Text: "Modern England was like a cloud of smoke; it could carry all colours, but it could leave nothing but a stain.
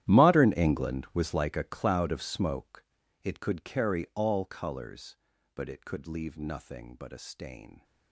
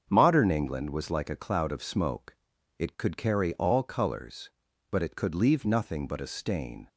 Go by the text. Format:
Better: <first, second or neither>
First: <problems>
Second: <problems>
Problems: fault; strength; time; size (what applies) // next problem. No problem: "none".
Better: second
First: gets quieter; strong; throughout; 18 dB // starts louder than the rest; strong; until 1.0 s; 12.5 dB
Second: starts louder than the rest; until 1.1 s; 7 dB